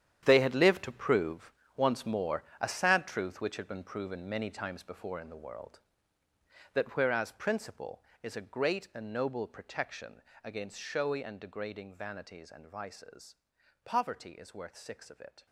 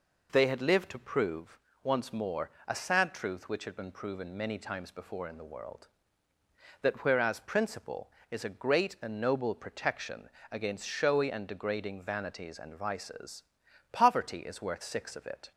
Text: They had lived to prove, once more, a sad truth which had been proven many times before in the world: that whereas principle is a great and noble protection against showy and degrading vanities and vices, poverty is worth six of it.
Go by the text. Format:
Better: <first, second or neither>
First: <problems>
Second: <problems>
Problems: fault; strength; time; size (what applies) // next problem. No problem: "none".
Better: second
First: gets quieter; strong; throughout; 13 dB // pauses between "protection" and "against"; slight; at 10.2 s; 0.22 s long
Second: pauses between "protection" and "against"; slight; at 10.2 s; 0.22 s long